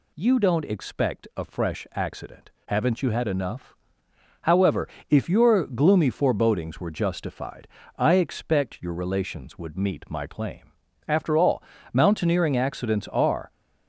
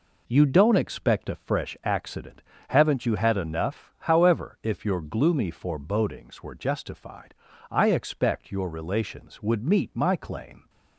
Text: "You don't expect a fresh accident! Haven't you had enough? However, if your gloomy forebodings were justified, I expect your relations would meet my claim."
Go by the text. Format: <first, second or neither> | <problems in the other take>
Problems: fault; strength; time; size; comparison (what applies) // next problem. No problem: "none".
second | goes on to say "After all mountaineering accidents are"; strong; from 11.0 s on; 2.4 s long